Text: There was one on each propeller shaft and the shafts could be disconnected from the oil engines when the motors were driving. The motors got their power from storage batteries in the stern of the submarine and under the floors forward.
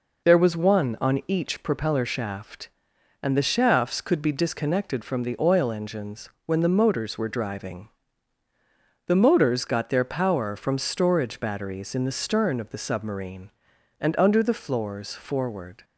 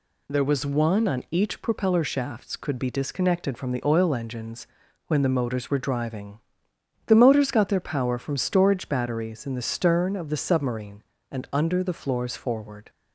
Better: first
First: pauses between "engines" and "when"; slight; at 6.2 s; 0.16 s long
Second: skips "shaft and the"; at 2.0 s // pauses between "engines" and "when"; at 4.6 s; 0.40 s long

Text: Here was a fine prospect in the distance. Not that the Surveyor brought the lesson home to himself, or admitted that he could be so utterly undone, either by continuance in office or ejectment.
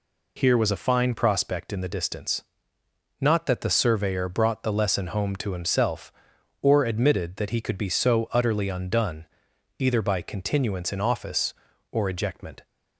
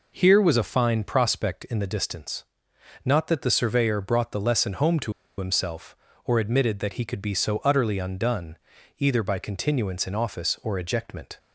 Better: first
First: none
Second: pauses between "to" and "himself"; slight; at 5.1 s; 0.26 s long

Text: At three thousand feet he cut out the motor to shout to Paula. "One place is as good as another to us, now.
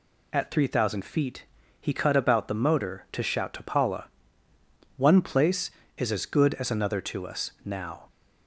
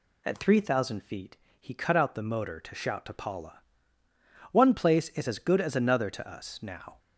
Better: second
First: pauses between "feet" and "he"; slight; at 1.4 s; 0.36 s long // says "about" for "out"; at 2.1 s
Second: pauses between "feet" and "he"; slight; at 1.3 s; 0.22 s long

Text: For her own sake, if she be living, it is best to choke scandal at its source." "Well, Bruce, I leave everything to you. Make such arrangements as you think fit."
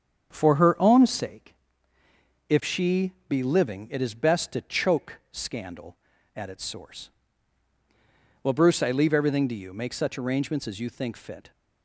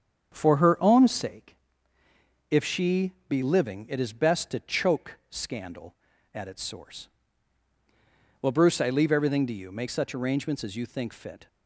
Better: neither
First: starts louder than the rest; strong; until 1.3 s; 7.5 dB // pauses between "she" and "be"; slight; at 3.1 s; 0.16 s long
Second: starts louder than the rest; strong; until 1.3 s; 7.5 dB // pauses between "she" and "be"; slight; at 3.1 s; 0.16 s long

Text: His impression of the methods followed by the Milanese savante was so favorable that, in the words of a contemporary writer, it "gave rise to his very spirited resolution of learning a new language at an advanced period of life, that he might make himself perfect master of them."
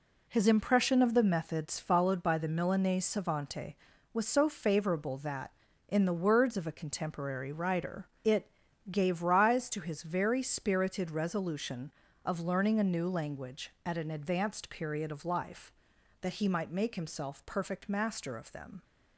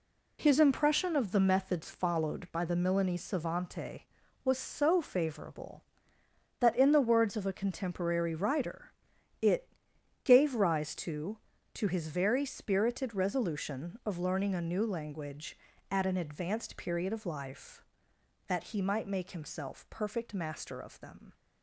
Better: first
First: pauses between "it" and "gave"; at 8.5 s; 0.40 s long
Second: pauses between "it" and "gave"; noticeable; at 9.6 s; 0.56 s long // says "to" twice; at 11.7 s

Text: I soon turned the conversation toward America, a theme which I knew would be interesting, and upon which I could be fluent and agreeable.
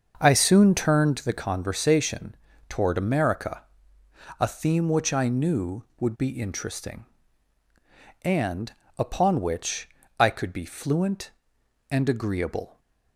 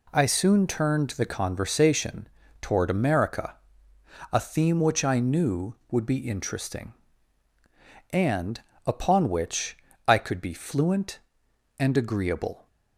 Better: second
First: starts louder than the rest; until 1.3 s; 6.5 dB // pauses between "conversation" and "toward"; slight; at 2.3 s; 0.34 s long // pauses between "and" and "upon"; slight; at 8.7 s; 0.24 s long // pauses between "which" and "I"; slight; at 9.8 s; 0.30 s long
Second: pauses between "conversation" and "toward"; slight; at 2.2 s; 0.34 s long // pauses between "and" and "upon"; slight; at 8.6 s; 0.24 s long // pauses between "which" and "I"; slight; at 9.7 s; 0.30 s long

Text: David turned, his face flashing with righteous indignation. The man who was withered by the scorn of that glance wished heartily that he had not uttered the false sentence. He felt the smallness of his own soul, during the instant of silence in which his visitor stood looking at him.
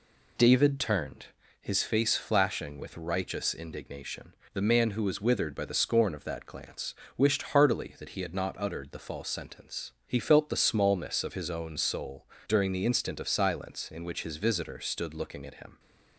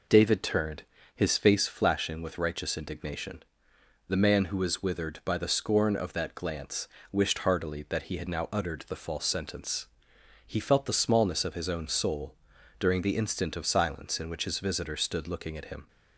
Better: first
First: pauses between "glance" and "wished"; slight; at 6.9 s; 0.24 s long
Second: pauses between "glance" and "wished"; slight; at 6.8 s; 0.24 s long // says "now" for "not"; at 8.2 s

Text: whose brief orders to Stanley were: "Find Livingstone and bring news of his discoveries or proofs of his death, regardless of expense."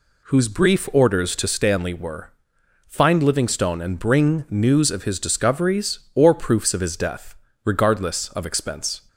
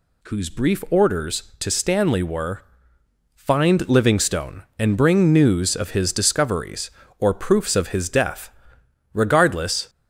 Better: first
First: none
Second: stops before "of expense"; at 9.8 s

